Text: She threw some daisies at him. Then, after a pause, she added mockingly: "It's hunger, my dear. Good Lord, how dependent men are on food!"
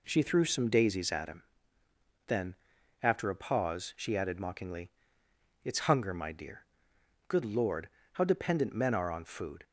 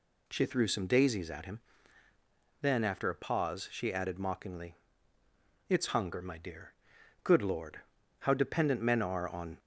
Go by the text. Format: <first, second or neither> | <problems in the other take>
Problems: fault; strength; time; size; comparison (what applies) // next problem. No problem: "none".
first | stops before "food"; at 9.5 s